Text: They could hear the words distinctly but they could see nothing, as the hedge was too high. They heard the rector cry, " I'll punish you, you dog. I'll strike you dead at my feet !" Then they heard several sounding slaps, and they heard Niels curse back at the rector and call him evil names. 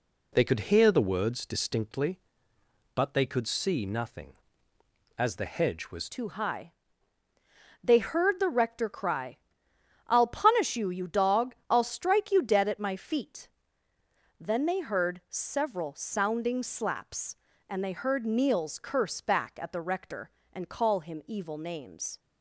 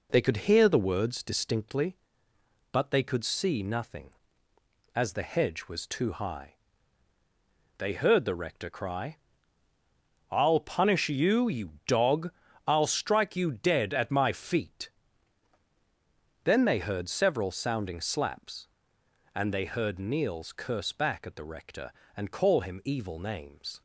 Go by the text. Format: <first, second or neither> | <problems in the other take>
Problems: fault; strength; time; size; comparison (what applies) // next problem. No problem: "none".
second | changes voice at "too"; from 6.0 s on; 16.1 s long